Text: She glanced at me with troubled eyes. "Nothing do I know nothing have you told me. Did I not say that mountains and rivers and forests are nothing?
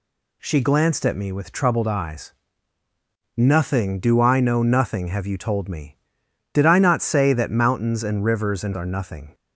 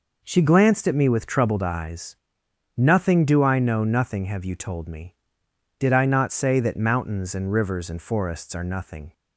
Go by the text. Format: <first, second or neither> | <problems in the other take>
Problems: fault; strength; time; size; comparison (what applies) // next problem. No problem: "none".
second | skips "forests"; at 8.7 s